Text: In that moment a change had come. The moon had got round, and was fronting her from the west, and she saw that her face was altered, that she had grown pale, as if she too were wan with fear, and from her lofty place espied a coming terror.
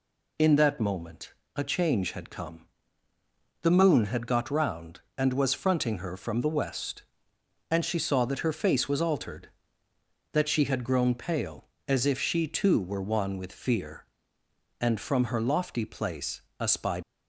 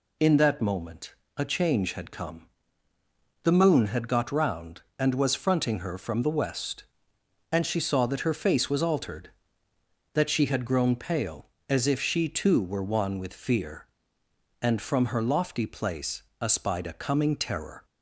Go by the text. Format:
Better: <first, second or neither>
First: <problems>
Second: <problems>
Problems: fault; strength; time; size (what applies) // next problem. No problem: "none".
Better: second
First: pauses between "moment" and "a"; slight; at 1.3 s; 0.24 s long // pauses between "place" and "espied"; slight; at 16.4 s; 0.18 s long // stops before "a coming terror"; at 17.0 s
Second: pauses between "moment" and "a"; slight; at 1.1 s; 0.24 s long // pauses between "place" and "espied"; slight; at 16.2 s; 0.18 s long